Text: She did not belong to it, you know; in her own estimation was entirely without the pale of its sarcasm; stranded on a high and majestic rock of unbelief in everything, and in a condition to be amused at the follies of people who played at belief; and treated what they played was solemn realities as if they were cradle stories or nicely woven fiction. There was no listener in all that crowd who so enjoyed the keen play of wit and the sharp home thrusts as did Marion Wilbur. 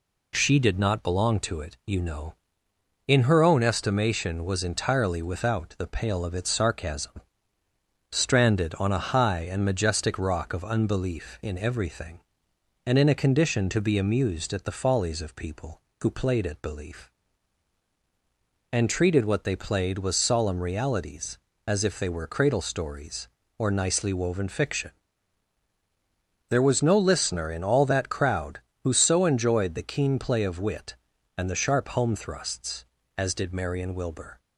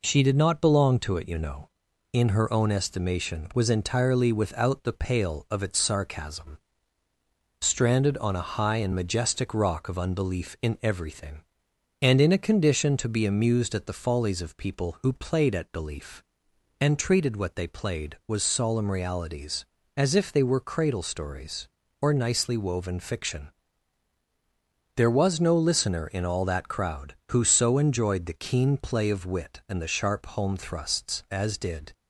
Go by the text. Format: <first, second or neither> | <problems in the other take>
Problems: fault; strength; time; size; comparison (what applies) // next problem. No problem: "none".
first | stops before "Marion Wilbur"; at 31.9 s